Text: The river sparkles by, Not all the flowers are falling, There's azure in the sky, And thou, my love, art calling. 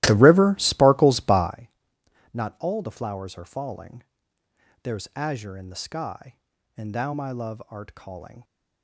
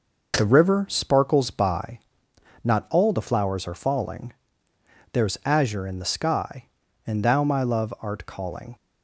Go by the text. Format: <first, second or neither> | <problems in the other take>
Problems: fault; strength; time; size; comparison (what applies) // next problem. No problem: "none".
second | starts louder than the rest; strong; until 1.5 s; 16.5 dB